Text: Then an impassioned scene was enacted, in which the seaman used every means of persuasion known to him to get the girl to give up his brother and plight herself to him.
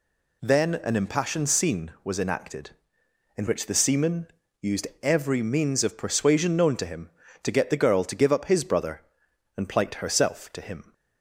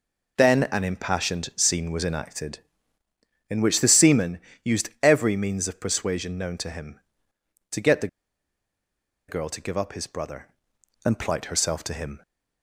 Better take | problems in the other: first | pauses between "seaman" and "used"; slight; at 4.3 s; 0.24 s long; slight in the first // pauses between "the" and "girl"; at 8.0 s; 1.2 s long

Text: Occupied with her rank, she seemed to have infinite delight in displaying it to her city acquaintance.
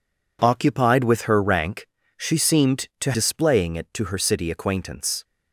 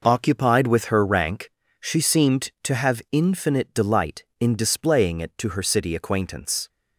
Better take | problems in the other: second | skips "have infinite delight in"; at 3.1 s

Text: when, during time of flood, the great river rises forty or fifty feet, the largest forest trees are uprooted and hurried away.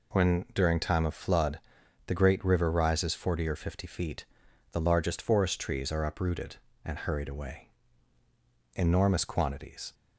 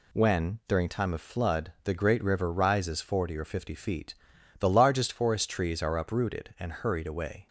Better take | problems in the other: second | goes on to say "Enormous quantities"; noticeable; from 8.7 s on; 1.1 s long

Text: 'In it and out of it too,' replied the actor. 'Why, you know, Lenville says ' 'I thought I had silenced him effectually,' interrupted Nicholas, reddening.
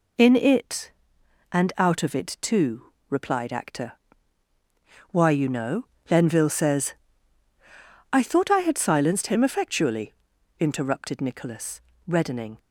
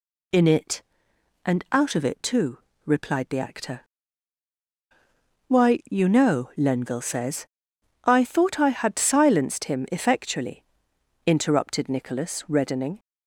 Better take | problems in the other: second | skips "the"; at 3.5 s

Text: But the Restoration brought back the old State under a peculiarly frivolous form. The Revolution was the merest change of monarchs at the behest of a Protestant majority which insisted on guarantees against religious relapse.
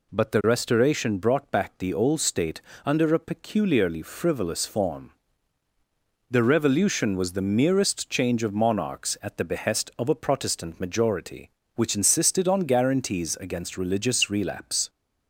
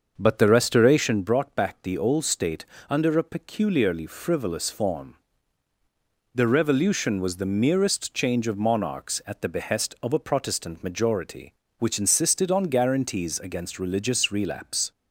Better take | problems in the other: first | starts louder than the rest; until 1.3 s; 6.5 dB // pauses between "State" and "under"; slight; at 2.6 s; 0.24 s long; slight in the first

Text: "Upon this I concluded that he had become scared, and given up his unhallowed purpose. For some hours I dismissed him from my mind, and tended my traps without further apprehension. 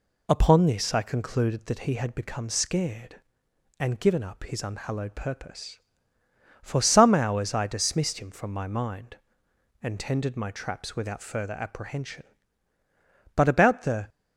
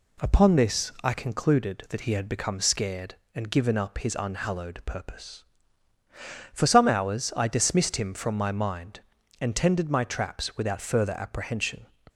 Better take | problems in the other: second | goes on to say "But about the"; noticeable; from 13.3 s on; 0.74 s long

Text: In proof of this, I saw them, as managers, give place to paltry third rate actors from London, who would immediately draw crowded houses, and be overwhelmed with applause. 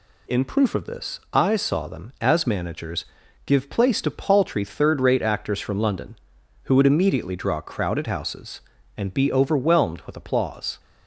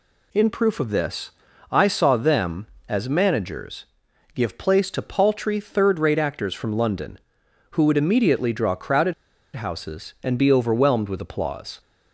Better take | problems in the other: first | pauses between "crowded" and "houses"; at 9.1 s; 0.42 s long

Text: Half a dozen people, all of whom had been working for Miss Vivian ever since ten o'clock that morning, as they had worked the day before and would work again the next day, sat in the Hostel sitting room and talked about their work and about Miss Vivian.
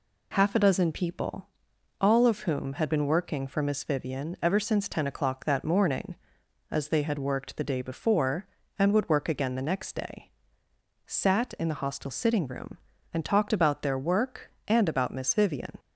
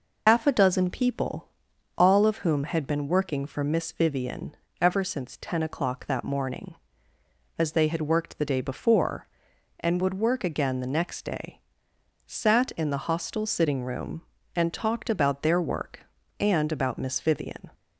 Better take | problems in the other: first | loses the start of "Half"; at 0.2 s; 90 ms // pauses between "Vivian" and "ever"; slight; at 4.5 s; 0.24 s long

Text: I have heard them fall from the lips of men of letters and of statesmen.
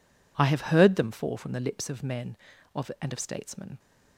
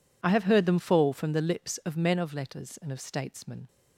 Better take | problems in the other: second | skips "letters"; at 2.9 s

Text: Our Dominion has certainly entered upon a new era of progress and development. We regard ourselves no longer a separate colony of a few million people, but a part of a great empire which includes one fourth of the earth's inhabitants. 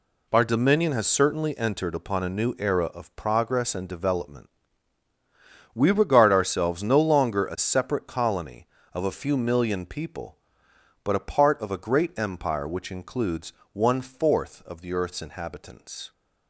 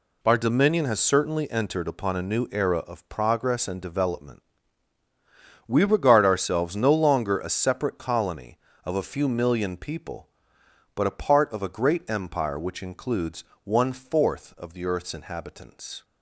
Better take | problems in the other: neither | pauses between "includes" and "one"; slight; the same in both

